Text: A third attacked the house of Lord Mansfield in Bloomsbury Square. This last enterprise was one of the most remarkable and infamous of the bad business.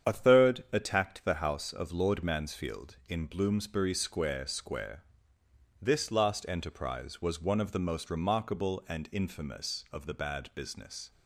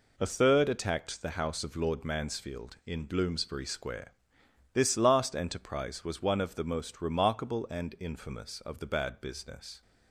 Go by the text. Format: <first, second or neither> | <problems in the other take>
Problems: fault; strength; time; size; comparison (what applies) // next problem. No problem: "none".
second | starts louder than the rest; strong; until 1.1 s; 8 dB // says "Square" twice; at 4.4 s